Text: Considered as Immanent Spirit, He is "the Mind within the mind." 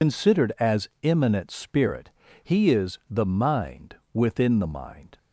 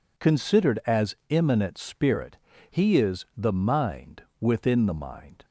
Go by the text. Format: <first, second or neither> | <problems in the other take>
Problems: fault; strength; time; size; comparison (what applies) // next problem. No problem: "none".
second | loses the start of "Considered"; at 0.0 s; 95 ms // pauses between "Mind" and "within"; slight; at 3.9 s; 0.18 s long; slight in the second